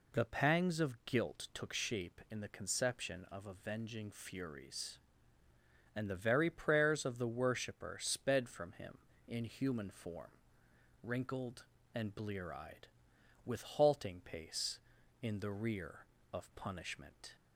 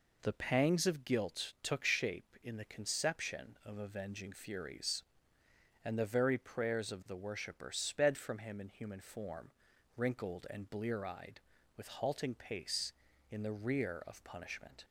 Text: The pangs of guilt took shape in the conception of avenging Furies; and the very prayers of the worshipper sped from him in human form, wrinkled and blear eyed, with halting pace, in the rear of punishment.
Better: neither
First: none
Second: none

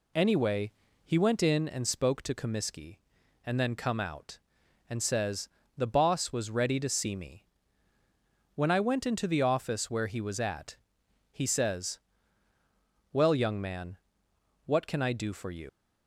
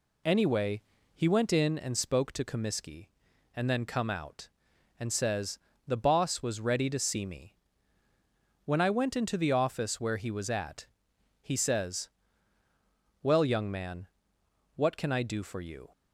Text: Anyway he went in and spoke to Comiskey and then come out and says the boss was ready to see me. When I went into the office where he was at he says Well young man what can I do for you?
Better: second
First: pauses between "Anyway" and "he"; slight; at 0.7 s; 0.32 s long // pauses between "says" and "the"; slight; at 5.4 s; 0.28 s long // pauses between "at" and "he"; noticeable; at 10.7 s; 0.56 s long // pauses between "says" and "Well"; at 11.9 s; 1.1 s long // pauses between "man" and "what"; noticeable; at 13.9 s; 0.68 s long // leaves "you" unfinished; at 15.6 s; 120 ms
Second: pauses between "Anyway" and "he"; slight; at 0.8 s; 0.32 s long // pauses between "says" and "the"; slight; at 5.5 s; 0.28 s long // pauses between "at" and "he"; noticeable; at 10.8 s; 0.56 s long // pauses between "says" and "Well"; at 12.0 s; 1.1 s long // pauses between "man" and "what"; noticeable; at 14.0 s; 0.68 s long

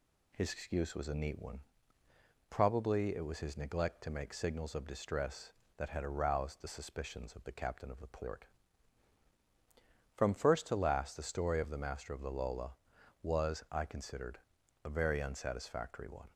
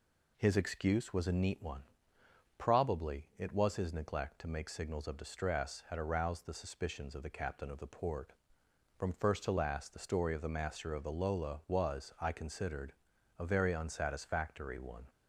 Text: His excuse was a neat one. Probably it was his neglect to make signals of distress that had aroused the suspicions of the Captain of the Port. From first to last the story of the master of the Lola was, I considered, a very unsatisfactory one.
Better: first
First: none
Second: skips "that"; at 5.8 s

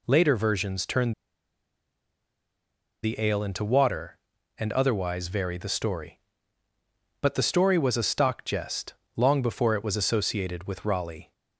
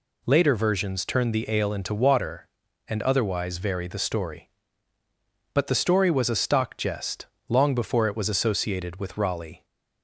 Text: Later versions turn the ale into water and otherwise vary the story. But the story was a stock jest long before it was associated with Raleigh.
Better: second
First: pauses between "turn" and "the"; strong; at 1.1 s; 1.9 s long // pauses between "jest" and "long"; slight; at 8.9 s; 0.20 s long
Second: pauses between "jest" and "long"; slight; at 7.2 s; 0.20 s long

